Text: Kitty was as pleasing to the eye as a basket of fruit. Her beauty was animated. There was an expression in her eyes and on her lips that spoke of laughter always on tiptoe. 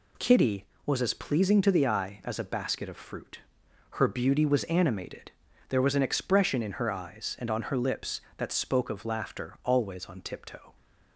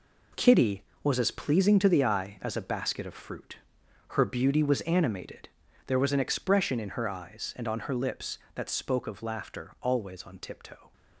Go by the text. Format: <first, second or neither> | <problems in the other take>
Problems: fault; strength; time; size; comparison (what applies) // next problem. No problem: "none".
first | gets quieter; strong; throughout; 9 dB